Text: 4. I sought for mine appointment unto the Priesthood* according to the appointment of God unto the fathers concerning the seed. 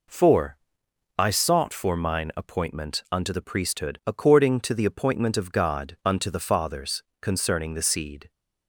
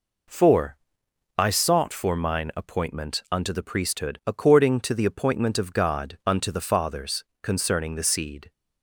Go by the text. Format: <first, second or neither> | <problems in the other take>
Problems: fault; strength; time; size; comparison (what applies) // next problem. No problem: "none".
neither | pauses between "fathers" and "concerning"; slight; the same in both